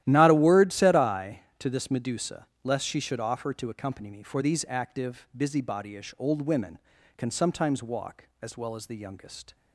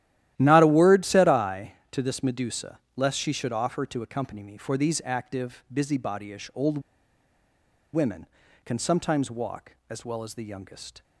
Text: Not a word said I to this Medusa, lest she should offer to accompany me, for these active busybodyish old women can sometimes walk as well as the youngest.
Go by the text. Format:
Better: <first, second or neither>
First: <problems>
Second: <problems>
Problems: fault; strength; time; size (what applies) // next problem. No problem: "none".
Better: first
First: starts louder than the rest; strong; until 1.0 s; 13 dB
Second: starts louder than the rest; strong; until 1.3 s; 13 dB // pauses between "old" and "women"; at 6.7 s; 1.1 s long